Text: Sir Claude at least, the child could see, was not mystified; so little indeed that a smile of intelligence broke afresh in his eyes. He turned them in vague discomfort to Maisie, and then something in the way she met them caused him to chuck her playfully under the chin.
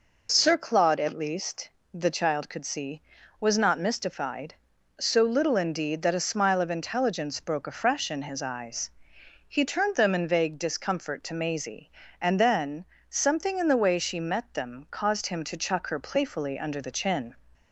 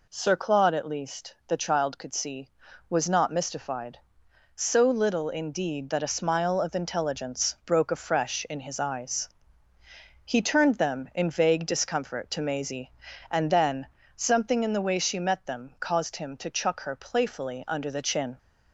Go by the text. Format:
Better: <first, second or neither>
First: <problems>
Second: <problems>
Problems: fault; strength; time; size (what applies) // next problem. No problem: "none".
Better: neither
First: pauses between "then" and "something"; slight; at 12.8 s; 0.24 s long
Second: pauses between "then" and "something"; slight; at 13.8 s; 0.30 s long